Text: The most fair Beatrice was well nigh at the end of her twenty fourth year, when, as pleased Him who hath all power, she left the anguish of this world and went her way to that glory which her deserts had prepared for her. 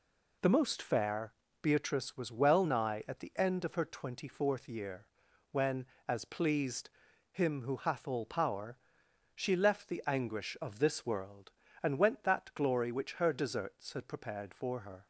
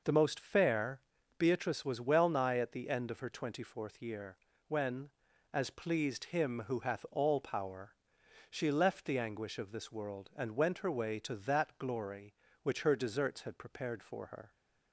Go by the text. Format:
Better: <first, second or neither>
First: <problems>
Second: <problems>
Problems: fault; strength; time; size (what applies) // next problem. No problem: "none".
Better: second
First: pauses between "fair" and "Beatrice"; slight; at 1.3 s; 0.31 s long // pauses between "pleased" and "Him"; at 6.8 s; 0.42 s long // skips "her way to"; at 12.2 s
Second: pauses between "fair" and "Beatrice"; at 1.0 s; 0.38 s long